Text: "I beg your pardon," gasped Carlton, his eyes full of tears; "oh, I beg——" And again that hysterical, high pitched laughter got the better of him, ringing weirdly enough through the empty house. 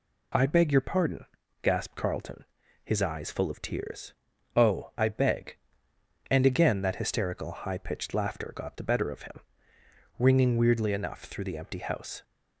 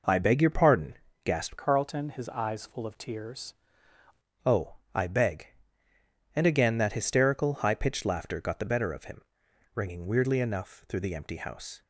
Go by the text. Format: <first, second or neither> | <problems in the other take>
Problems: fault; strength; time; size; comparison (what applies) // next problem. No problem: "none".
first | changes voice from "Carlton" to "tears"; from 1.5 to 3.5 s; 2.0 s long